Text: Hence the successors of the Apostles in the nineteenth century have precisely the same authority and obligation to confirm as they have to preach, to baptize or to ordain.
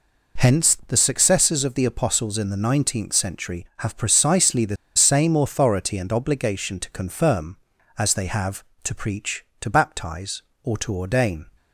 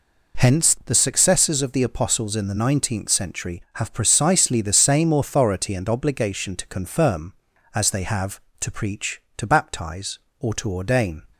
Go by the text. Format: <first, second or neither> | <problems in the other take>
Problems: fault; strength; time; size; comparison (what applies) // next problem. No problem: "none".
second | pauses between "the" and "same"; slight; at 4.7 s; 0.20 s long